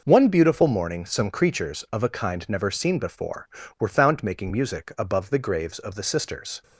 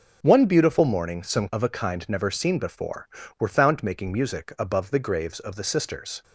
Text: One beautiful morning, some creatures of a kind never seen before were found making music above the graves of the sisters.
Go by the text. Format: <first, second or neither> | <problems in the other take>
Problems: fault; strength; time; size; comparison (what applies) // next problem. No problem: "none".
first | starts louder than the rest; until 1.2 s; 6.5 dB // skips "creatures"; at 1.5 s